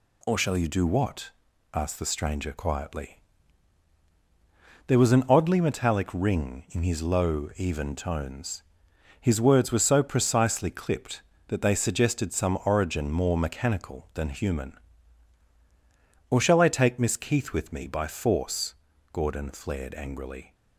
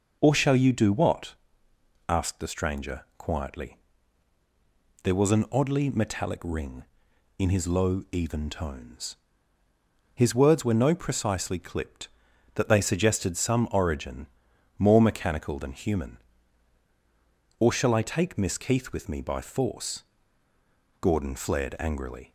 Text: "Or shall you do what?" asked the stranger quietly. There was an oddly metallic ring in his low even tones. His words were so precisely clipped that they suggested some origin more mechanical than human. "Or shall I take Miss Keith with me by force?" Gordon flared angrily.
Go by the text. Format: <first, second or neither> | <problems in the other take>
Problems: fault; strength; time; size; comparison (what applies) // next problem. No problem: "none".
first | says "no" for "so"; at 10.8 s // pauses between "origin" and "more"; noticeable; at 14.2 s; 0.52 s long